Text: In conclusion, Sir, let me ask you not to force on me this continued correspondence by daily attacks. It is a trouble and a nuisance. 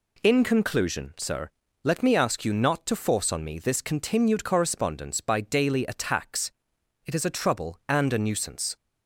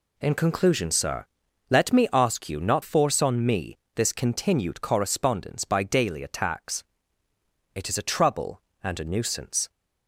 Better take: first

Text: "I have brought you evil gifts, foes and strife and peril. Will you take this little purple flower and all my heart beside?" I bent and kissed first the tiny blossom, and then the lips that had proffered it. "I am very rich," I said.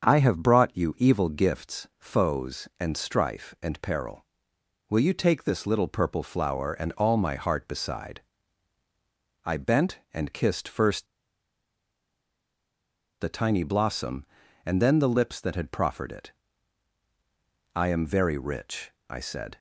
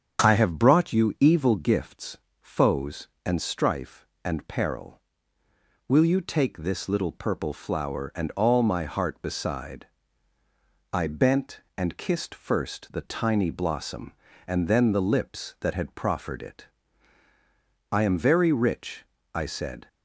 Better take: second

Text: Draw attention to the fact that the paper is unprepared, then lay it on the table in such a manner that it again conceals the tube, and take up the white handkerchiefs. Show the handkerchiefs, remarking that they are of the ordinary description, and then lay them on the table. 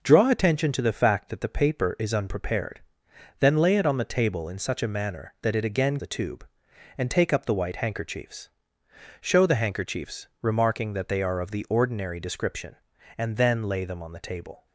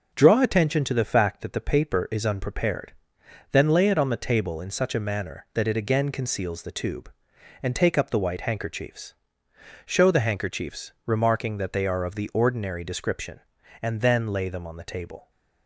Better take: second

